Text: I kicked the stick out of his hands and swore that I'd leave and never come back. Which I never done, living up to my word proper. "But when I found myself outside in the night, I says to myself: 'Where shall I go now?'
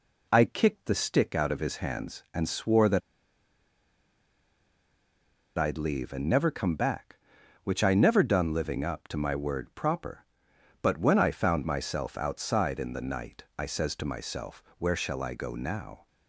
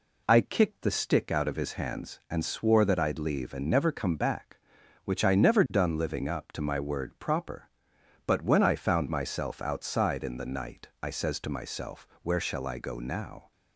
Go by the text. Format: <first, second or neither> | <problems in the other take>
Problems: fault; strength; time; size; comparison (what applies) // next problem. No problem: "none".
second | pauses between "that" and "I'd"; strong; at 3.0 s; 2.5 s long